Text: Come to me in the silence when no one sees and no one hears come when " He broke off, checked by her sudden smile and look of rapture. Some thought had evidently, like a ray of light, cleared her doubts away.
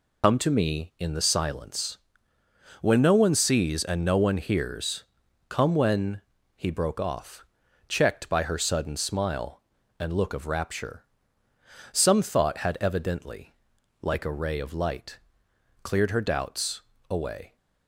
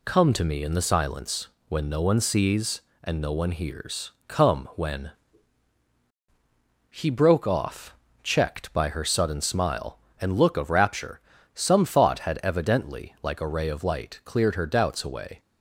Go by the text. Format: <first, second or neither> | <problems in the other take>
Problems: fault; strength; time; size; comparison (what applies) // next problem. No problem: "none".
second | loses the start of "Come"; at 0.2 s; 65 ms // pauses between "silence" and "when"; noticeable; at 1.9 s; 0.84 s long; slight in the second // pauses between "hears" and "come"; noticeable; at 5.0 s; 0.46 s long; slight in the second // pauses between "doubts" and "away"; slight; at 16.8 s; 0.28 s long